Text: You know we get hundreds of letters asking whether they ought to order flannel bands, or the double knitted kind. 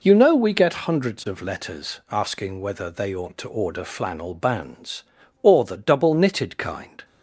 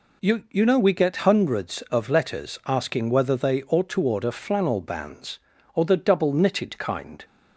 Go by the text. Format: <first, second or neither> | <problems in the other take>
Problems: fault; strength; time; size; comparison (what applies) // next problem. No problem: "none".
first | says "You" twice; at 0.4 s